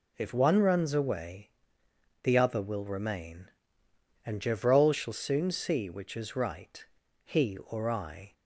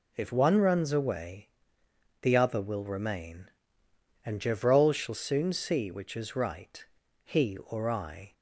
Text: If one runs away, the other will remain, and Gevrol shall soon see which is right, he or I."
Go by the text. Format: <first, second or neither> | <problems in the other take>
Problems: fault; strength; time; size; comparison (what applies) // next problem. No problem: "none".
neither | none